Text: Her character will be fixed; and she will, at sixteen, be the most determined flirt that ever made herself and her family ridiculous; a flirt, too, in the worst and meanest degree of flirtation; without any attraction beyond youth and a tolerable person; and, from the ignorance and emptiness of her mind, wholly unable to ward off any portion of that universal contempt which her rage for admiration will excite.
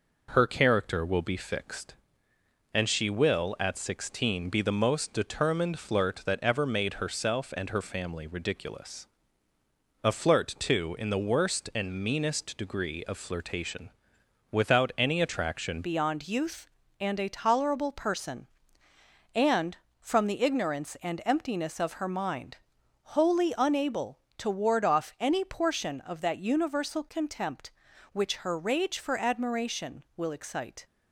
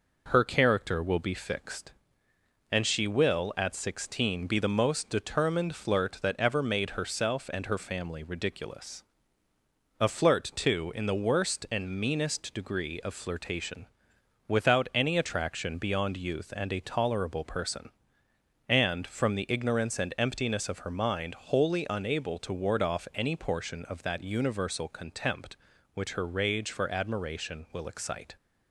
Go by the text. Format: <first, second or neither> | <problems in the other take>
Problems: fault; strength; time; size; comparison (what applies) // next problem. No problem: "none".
second | changes voice at "beyond"; from 15.8 s on; 15.0 s long